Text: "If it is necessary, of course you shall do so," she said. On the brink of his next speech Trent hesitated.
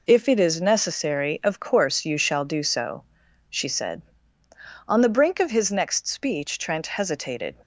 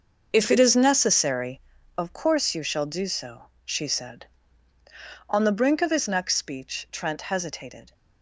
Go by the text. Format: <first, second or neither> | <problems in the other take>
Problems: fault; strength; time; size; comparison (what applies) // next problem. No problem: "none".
first | starts louder than the rest; until 2.2 s; 6 dB